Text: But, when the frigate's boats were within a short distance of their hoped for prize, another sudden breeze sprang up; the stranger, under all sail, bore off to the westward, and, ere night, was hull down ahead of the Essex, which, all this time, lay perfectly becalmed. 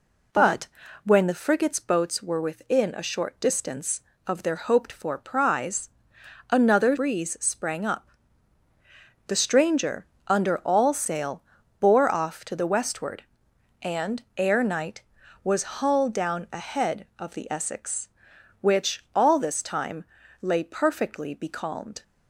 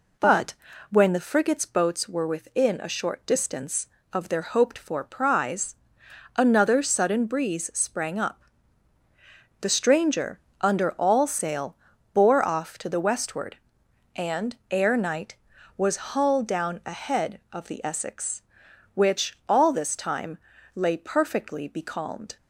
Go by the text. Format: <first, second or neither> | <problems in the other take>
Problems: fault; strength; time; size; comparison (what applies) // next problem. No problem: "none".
second | skips "sudden"; at 6.9 s